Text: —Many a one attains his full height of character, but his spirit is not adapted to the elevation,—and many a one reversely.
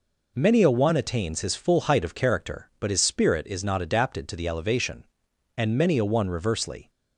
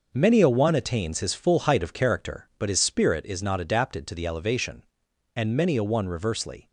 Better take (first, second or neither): first